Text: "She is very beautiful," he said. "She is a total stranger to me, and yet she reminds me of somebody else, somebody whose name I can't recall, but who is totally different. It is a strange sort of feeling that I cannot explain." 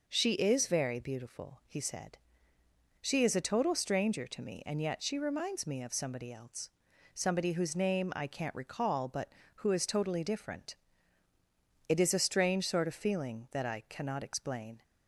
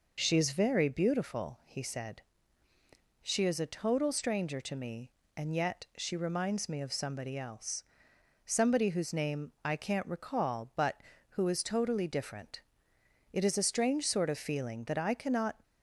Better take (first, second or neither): first